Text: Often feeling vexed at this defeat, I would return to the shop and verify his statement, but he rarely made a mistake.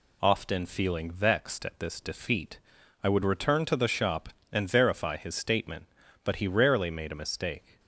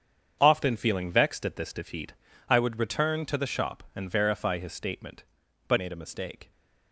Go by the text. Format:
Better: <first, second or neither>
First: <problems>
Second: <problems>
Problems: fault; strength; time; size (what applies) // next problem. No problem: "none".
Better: first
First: none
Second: starts louder than the rest; strong; until 1.4 s; 7.5 dB // skips "he rarely"; at 5.7 s